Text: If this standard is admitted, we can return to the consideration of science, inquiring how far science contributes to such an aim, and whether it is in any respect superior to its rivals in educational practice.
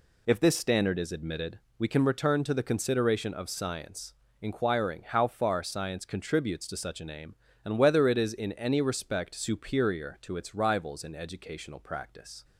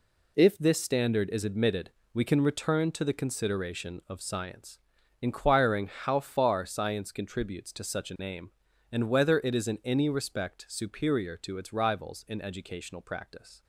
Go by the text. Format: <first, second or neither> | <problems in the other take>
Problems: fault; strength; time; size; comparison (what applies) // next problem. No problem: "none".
neither | none